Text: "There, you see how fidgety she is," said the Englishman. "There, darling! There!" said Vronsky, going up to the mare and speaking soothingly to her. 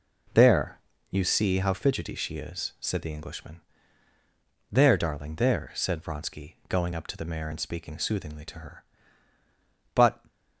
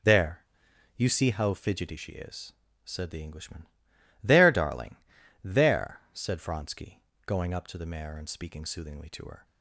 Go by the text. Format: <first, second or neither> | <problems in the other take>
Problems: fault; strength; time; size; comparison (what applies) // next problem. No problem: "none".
second | goes on to say "But"; slight; from 9.9 s on; 0.26 s long